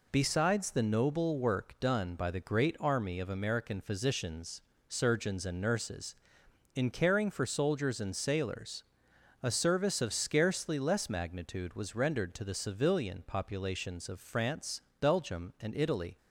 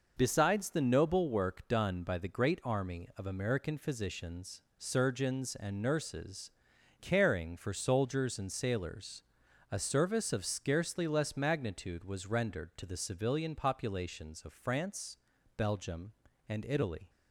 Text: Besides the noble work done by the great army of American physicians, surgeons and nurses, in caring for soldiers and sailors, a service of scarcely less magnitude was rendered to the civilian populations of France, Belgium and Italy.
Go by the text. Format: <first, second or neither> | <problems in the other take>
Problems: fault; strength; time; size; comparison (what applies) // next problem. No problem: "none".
first | skips "in"; at 6.7 s